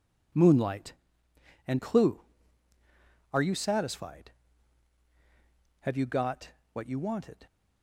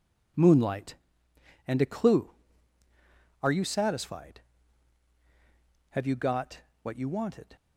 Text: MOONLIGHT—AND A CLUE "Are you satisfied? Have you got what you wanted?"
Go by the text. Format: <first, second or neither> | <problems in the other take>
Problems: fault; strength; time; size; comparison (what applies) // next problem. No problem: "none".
second | skips "A"; at 1.7 s // pauses between "got" and "what"; slight; at 6.4 s; 0.24 s long; slight in the second